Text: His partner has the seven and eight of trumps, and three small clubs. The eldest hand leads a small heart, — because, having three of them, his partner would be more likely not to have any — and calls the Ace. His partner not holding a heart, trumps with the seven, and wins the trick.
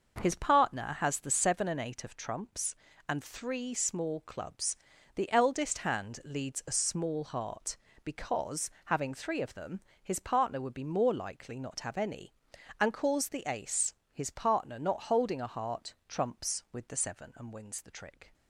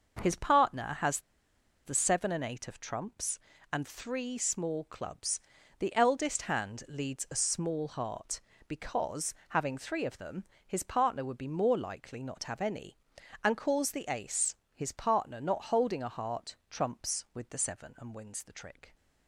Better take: first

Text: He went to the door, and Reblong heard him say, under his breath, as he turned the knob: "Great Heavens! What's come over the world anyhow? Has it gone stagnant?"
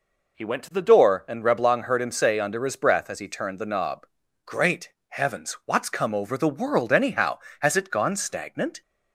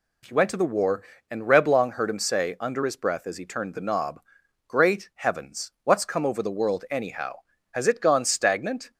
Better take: first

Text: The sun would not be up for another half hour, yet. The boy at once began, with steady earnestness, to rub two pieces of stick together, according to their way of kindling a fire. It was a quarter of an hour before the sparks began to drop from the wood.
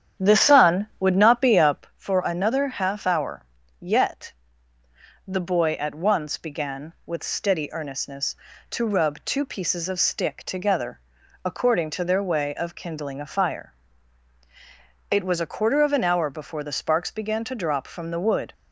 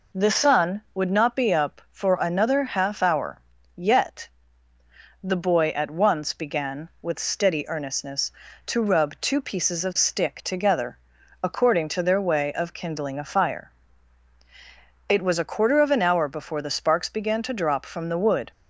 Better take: second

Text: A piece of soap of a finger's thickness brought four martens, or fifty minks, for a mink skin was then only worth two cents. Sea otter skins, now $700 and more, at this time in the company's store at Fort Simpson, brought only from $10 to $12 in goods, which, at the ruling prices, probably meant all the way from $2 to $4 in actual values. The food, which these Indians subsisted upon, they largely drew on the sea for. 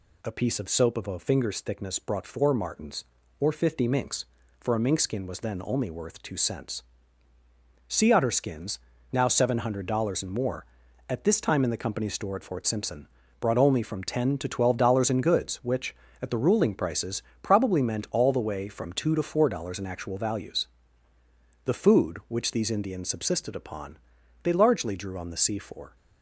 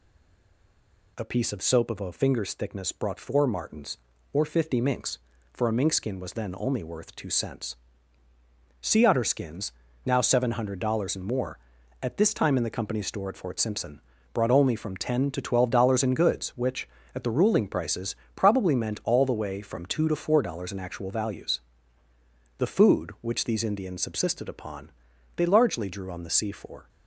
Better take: first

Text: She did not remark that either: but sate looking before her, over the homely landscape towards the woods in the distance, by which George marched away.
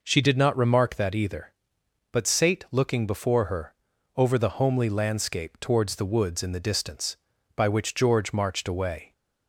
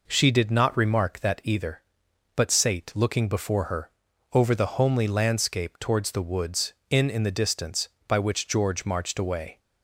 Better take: first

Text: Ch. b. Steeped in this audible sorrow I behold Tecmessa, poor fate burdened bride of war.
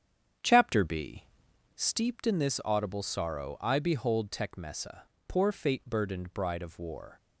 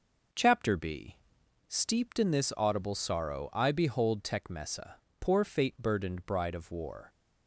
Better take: second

